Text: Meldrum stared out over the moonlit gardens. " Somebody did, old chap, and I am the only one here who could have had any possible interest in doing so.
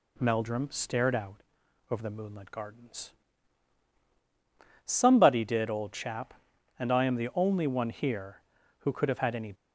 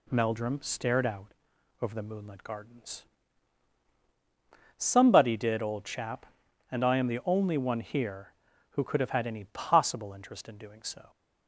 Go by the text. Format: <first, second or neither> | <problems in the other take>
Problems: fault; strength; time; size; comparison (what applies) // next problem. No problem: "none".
second | pauses between "out" and "over"; noticeable; at 1.4 s; 0.48 s long; noticeable in the second // stops before "possible interest in doing so"; at 9.5 s